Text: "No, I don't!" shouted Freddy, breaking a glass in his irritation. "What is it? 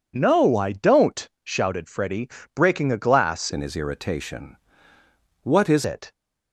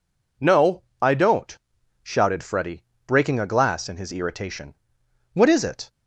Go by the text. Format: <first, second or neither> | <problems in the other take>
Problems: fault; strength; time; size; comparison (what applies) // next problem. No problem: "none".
second | changes voice from "in" to "is"; from 3.5 to 5.8 s; 2.3 s long